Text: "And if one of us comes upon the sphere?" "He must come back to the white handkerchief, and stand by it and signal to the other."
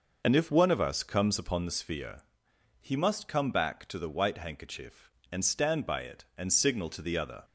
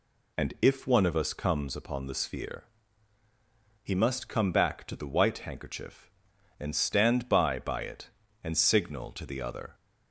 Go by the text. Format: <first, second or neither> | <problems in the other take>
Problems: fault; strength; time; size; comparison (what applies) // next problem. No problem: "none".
first | says "by" twice; at 7.5 s